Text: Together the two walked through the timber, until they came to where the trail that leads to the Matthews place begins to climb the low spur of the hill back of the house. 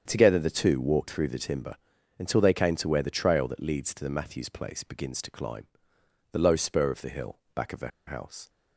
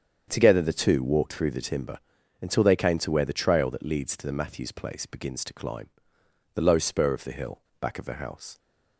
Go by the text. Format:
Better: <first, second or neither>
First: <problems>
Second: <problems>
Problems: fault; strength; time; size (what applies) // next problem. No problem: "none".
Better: second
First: starts louder than the rest; strong; until 1.0 s; 7.5 dB // pauses between "climb" and "the"; noticeable; at 5.6 s; 0.64 s long // pauses between "hill" and "back"; slight; at 7.3 s; 0.16 s long // pauses between "the" and "house"; slight; at 7.8 s; 0.18 s long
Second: starts louder than the rest; strong; until 1.2 s; 7.5 dB // pauses between "climb" and "the"; noticeable; at 5.8 s; 0.64 s long // pauses between "hill" and "back"; slight; at 7.6 s; 0.19 s long